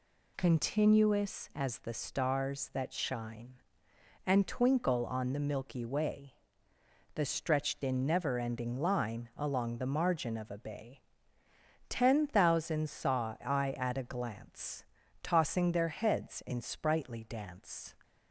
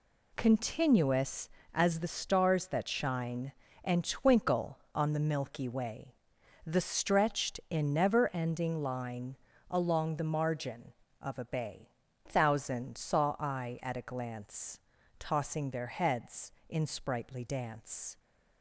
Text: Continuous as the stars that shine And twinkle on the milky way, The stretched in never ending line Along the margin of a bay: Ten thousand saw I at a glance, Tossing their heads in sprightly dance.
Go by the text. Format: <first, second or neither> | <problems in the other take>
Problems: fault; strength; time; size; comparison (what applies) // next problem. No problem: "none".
first | pauses between "line" and "Along"; slight; at 9.3 s; 0.34 s long // skips "Ten"; at 12.0 s